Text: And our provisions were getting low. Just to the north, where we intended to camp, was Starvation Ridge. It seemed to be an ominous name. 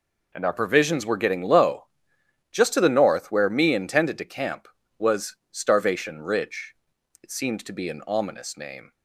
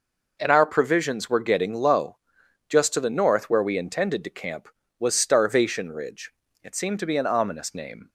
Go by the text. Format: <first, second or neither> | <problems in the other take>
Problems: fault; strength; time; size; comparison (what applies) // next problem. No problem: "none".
second | says "me" for "we"; at 3.4 s // pauses between "was" and "Starvation"; slight; at 5.3 s; 0.16 s long